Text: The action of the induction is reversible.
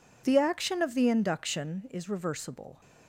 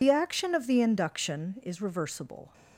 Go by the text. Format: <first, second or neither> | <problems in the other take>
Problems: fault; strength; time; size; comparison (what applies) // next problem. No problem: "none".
first | loses the start of "The"; at 0.0 s; 45 ms